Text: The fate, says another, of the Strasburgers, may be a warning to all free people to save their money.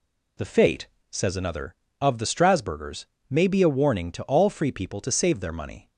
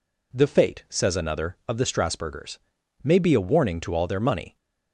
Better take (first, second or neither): first